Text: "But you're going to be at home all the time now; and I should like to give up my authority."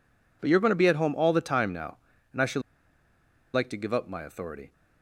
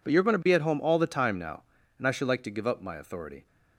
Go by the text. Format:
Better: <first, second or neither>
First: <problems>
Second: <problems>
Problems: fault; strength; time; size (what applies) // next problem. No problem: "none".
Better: second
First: pauses between "should" and "like"; noticeable; at 2.6 s; 0.92 s long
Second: none